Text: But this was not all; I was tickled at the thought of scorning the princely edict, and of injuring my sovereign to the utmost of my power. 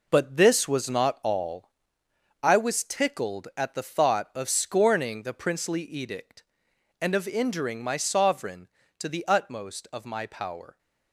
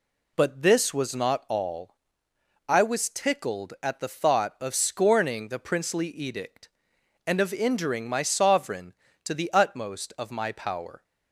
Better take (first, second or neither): second